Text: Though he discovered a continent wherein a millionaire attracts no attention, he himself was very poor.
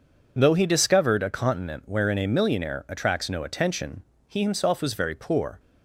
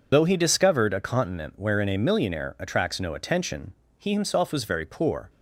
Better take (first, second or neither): first